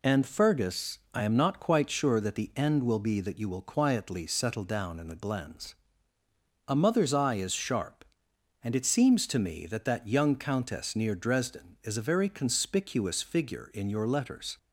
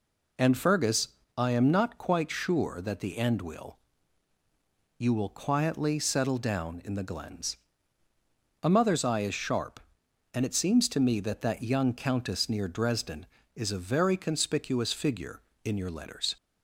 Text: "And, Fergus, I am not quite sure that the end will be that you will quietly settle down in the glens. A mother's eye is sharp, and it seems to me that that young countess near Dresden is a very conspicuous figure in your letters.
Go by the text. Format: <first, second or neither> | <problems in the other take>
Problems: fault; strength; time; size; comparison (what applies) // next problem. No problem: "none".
first | skips "be that"; at 4.3 s